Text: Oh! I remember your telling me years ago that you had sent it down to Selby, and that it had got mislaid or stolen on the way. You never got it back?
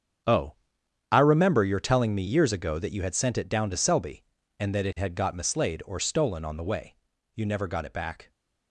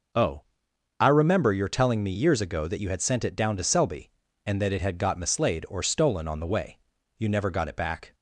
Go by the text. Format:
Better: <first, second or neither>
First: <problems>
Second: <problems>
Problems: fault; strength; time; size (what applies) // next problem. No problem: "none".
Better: second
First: gets quieter; strong; throughout; 13 dB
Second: none